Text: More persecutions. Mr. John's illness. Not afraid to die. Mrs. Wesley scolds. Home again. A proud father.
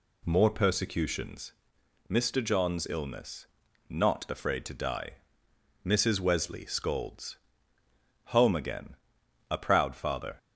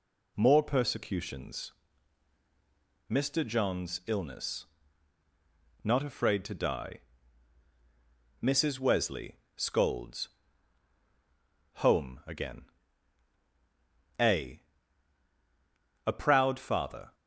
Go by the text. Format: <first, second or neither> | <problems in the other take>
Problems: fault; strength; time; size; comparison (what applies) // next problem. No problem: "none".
first | pauses between "Wesley" and "scolds"; slight; at 9.3 s; 0.20 s long // says "A" twice; at 16.0 s